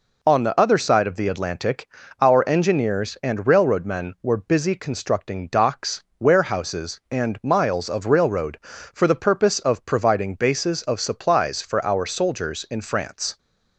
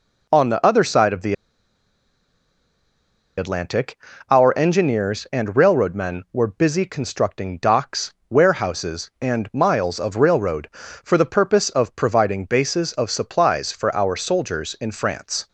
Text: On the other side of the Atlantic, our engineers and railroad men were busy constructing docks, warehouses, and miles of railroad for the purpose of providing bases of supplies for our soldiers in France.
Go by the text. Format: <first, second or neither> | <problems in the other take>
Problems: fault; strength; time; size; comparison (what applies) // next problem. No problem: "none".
first | pauses between "the" and "Atlantic"; strong; at 1.3 s; 2.0 s long